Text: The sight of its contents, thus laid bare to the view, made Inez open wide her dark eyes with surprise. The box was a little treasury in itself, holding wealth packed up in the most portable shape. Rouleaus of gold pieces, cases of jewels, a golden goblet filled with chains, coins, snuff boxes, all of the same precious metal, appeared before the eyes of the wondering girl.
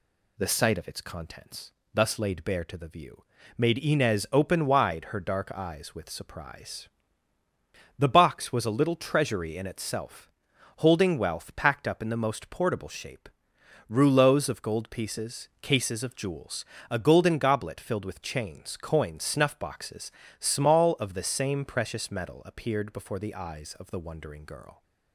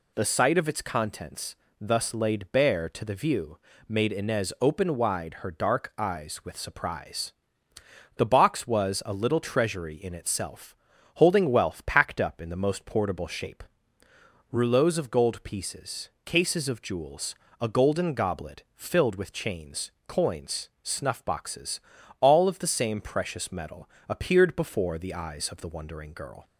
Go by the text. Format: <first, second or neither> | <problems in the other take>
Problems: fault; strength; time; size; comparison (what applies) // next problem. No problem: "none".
second | says "small" for "all"; at 20.3 s